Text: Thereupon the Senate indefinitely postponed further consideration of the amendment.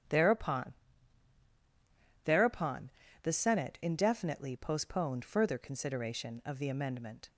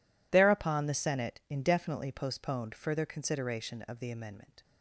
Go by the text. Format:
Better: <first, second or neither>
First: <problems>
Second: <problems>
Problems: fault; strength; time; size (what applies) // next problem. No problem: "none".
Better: second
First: starts louder than the rest; strong; until 2.5 s; 9.5 dB // says "Thereupon" twice; at 2.2 s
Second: none